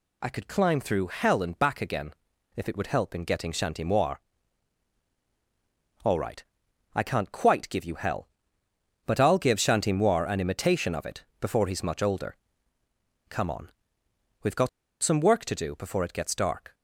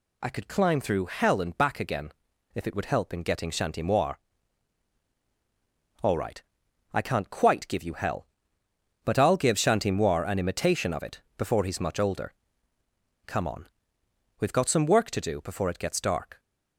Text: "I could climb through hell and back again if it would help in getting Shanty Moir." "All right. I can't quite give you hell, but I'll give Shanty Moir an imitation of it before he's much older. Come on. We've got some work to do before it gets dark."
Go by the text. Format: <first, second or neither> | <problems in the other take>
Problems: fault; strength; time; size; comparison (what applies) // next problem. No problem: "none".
second | pauses between "again" and "if"; at 2.1 s; 0.42 s long; also in the second // pauses between "got" and "some"; slight; at 14.6 s; 0.34 s long